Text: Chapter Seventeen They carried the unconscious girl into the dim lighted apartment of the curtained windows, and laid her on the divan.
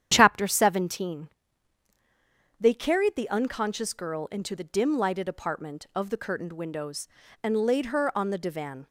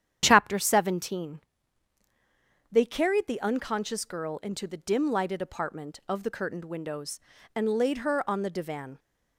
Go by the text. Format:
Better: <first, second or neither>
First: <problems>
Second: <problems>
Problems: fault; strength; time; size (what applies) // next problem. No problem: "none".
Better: neither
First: starts louder than the rest; strong; until 1.1 s; 9 dB // pauses between "Seventeen" and "They"; strong; at 1.3 s; 1.3 s long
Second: starts louder than the rest; strong; until 1.2 s; 9.5 dB // pauses between "Seventeen" and "They"; strong; at 1.4 s; 1.3 s long